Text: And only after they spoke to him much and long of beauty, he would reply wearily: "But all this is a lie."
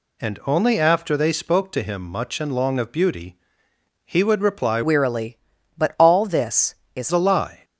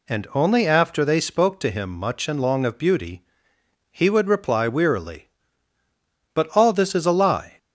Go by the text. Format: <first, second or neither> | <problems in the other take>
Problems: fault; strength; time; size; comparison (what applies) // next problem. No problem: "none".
second | changes voice from "wearily" to "is"; from 4.8 to 7.1 s; 2.3 s long